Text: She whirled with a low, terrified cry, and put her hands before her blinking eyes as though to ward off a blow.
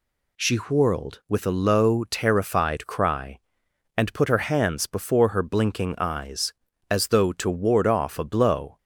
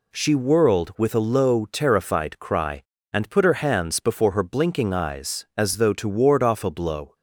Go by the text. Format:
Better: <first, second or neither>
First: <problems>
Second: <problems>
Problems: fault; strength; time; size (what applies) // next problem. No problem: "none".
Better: neither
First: none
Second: none